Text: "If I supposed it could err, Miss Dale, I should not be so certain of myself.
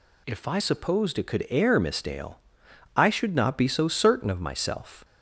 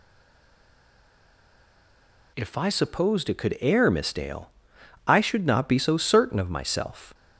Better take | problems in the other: first | stays silent before the first word; until 2.3 s; 2.3 s long

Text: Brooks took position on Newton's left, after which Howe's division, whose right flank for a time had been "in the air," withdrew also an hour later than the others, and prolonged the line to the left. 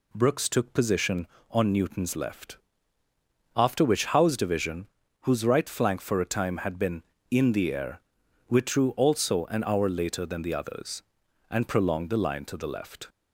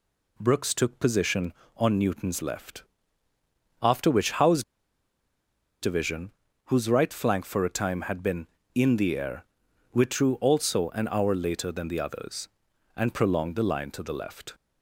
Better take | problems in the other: first | pauses between "Howe's" and "division"; at 4.6 s; 1.1 s long

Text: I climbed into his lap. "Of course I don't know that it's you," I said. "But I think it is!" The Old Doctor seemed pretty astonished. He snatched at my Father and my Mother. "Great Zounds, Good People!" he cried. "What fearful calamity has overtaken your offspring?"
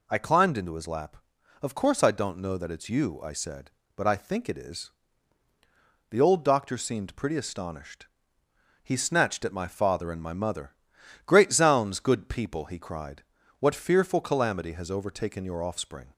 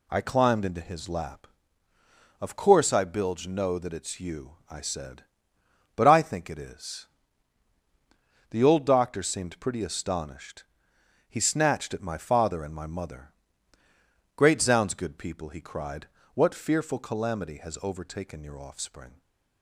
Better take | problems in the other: first | says "bilge" for "don't"; at 3.0 s // stays silent after the last word; slight; from 19.0 s on; 0.6 s long

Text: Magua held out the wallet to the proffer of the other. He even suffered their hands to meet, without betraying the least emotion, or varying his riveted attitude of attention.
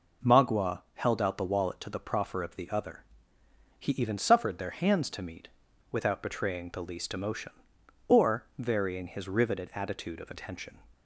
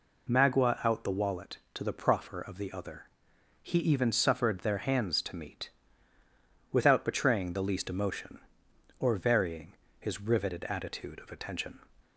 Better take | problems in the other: first | skips "held"; at 0.8 s // pauses between "varying" and "his"; slight; at 9.7 s; 0.26 s long

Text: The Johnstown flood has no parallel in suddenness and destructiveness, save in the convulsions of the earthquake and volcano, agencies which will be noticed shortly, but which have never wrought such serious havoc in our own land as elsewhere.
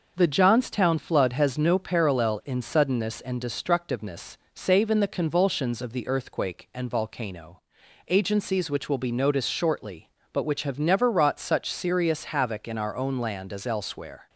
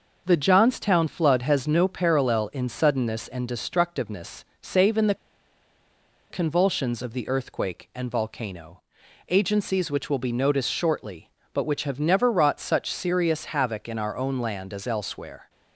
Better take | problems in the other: first | pauses between "the" and "convulsions"; at 5.1 s; 1.1 s long

